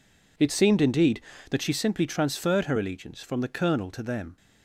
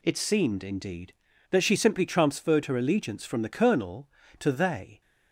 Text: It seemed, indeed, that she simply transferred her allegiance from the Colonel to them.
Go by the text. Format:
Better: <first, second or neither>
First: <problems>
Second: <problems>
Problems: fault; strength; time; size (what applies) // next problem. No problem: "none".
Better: first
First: none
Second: says "they" for "them"; at 4.5 s